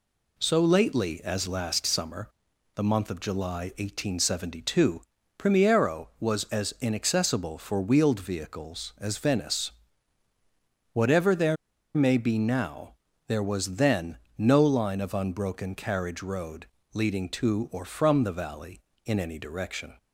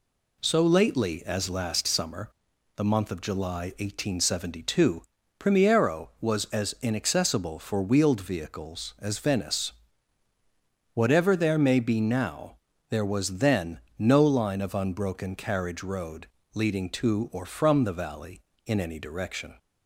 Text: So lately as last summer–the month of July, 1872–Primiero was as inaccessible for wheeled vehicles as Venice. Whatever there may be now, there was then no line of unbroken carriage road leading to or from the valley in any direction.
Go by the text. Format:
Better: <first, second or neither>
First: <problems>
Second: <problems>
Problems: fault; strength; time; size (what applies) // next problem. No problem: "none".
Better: second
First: pauses between "there" and "may"; at 11.5 s; 0.39 s long // pauses between "then" and "no"; slight; at 14.1 s; 0.20 s long // pauses between "road" and "leading"; slight; at 16.6 s; 0.28 s long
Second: pauses between "then" and "no"; slight; at 13.7 s; 0.18 s long // pauses between "road" and "leading"; slight; at 16.2 s; 0.28 s long